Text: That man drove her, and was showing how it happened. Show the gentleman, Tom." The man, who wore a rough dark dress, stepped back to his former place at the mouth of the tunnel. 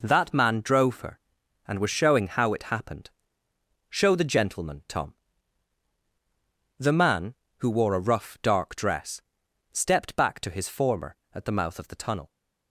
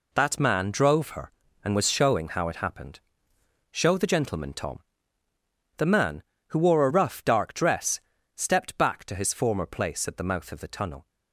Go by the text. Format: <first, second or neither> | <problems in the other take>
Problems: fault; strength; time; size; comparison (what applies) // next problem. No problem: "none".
second | skips "place"; at 11.2 s